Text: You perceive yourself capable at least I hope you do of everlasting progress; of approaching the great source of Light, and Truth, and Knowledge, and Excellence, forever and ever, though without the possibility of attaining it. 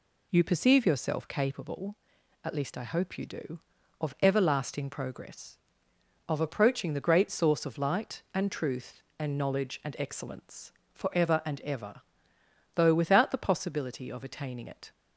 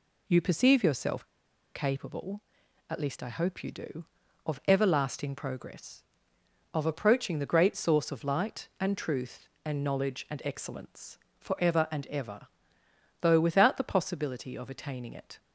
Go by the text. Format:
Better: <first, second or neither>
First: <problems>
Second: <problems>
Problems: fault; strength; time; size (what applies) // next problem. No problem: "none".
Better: first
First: none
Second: pauses between "yourself" and "capable"; noticeable; at 1.2 s; 0.50 s long